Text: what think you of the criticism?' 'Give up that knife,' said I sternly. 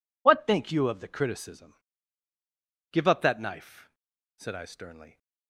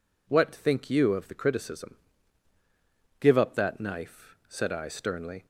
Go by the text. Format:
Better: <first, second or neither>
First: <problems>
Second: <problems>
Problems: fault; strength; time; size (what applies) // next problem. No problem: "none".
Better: neither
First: none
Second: none